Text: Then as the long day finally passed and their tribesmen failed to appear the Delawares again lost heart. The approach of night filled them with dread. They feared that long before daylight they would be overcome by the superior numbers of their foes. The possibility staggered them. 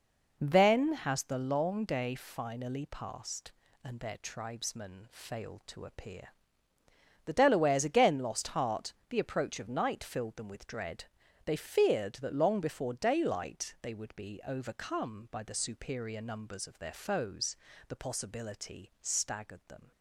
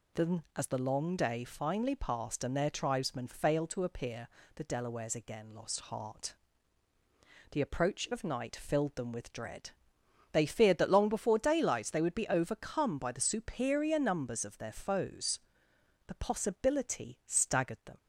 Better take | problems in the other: second | says "has" for "as"; at 0.9 s // pauses between "appear" and "the"; noticeable; at 6.2 s; 0.96 s long; slight in the second

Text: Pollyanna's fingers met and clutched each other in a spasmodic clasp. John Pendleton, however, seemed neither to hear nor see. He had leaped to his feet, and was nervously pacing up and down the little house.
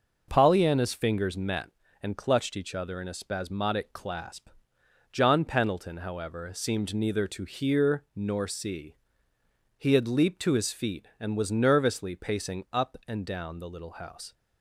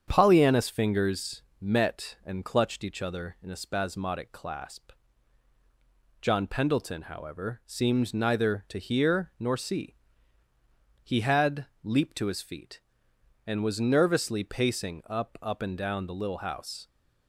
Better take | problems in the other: first | starts louder than the rest; strong; until 1.0 s; 8 dB // pauses between "fingers" and "met"; slight; at 1.4 s; 0.18 s long // pauses between "had" and "leaped"; slight; at 11.6 s; 0.16 s long // says "up" twice; at 15.4 s

